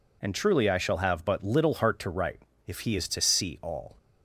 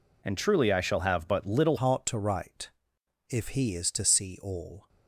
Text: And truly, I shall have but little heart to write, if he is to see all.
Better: first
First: none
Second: changes voice at "heart"; from 1.7 s on; 3.1 s long

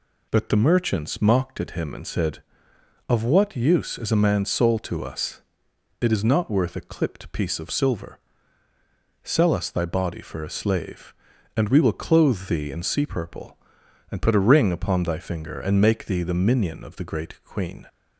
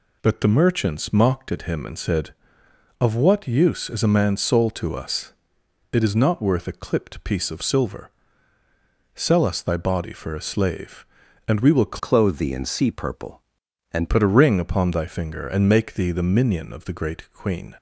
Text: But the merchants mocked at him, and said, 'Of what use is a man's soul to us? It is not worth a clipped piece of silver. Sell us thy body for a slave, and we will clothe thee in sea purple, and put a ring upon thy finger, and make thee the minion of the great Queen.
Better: first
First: none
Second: changes voice from "clothe" to "and"; from 11.9 to 14.0 s; 2.1 s long

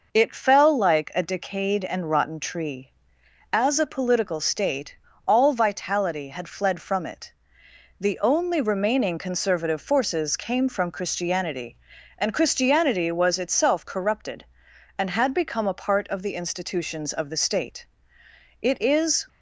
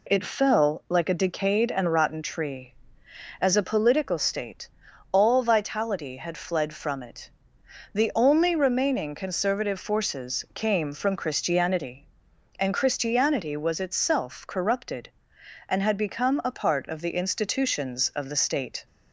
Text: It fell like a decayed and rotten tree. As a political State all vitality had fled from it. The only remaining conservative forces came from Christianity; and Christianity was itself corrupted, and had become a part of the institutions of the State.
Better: second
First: pauses between "State" and "all"; slight; at 4.9 s; 0.32 s long // goes on to say "It is"; noticeable; from 18.5 s on; 0.68 s long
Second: pauses between "State" and "all"; at 4.6 s; 0.42 s long

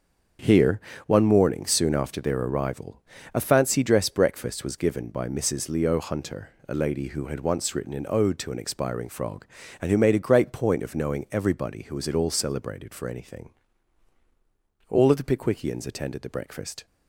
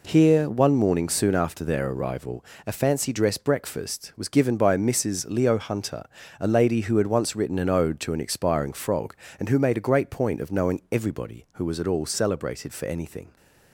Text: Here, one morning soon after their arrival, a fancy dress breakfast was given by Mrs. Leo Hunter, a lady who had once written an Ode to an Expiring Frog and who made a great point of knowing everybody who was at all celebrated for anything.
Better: second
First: starts louder than the rest; until 1.6 s; 7 dB // goes on to say "All of the Pickwickians attended the breakfast"; strong; from 14.8 s on; 1.9 s long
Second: none

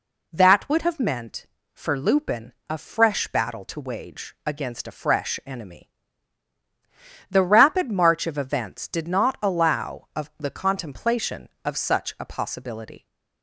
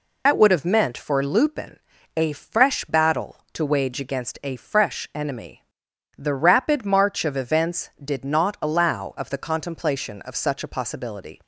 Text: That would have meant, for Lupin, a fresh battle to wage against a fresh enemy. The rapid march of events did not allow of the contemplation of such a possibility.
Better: first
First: none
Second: loses the start of "That"; at 0.2 s; 65 ms

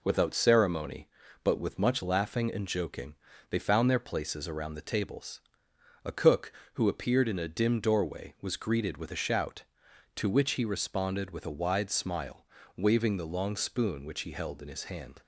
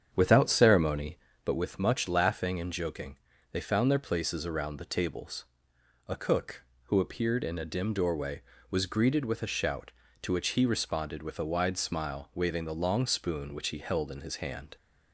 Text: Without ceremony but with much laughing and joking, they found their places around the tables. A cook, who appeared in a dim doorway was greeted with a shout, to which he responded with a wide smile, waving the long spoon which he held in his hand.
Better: first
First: none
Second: starts louder than the rest; strong; until 1.6 s; 8 dB

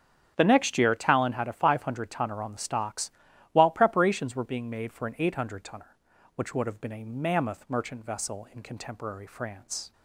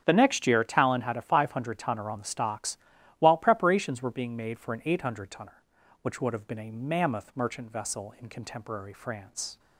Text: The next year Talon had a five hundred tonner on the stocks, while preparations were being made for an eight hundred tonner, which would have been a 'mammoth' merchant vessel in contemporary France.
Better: neither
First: starts louder than the rest; strong; until 1.3 s; 8 dB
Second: starts louder than the rest; strong; until 1.0 s; 8 dB

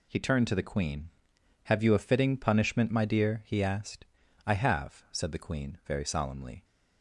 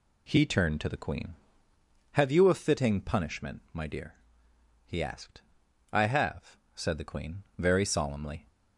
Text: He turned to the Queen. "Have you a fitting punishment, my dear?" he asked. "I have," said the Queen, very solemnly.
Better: neither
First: none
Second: none

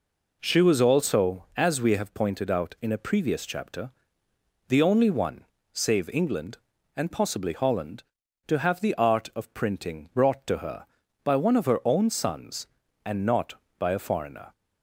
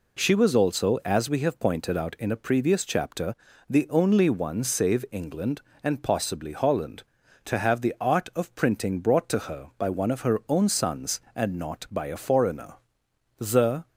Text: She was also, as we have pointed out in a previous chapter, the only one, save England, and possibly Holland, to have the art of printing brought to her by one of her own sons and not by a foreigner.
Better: first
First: none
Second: goes on to say "The"; from 13.3 s on; 0.50 s long

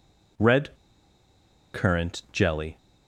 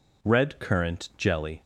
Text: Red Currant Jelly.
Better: second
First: pauses between "Red" and "Currant"; at 0.7 s; 0.98 s long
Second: none

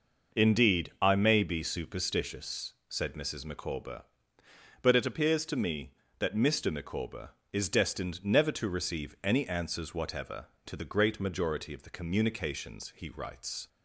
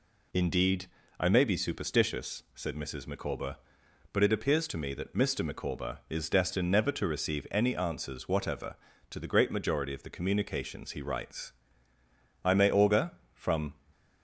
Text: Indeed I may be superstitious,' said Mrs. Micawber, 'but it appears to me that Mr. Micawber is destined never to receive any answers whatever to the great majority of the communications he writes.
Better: first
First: none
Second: pauses between "Indeed" and "I"; slight; at 0.8 s; 0.32 s long // goes on to say "I may augur from"; from 12.4 s on; 1.3 s long

